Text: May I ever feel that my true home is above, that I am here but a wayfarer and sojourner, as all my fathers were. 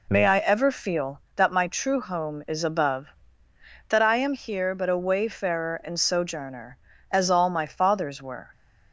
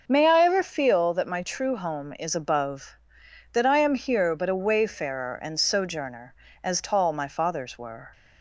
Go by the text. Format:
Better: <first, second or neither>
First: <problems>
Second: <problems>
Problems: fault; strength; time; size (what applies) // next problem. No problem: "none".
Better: first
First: none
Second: starts louder than the rest; until 1.0 s; 6.5 dB // says "tall" for "all"; at 6.7 s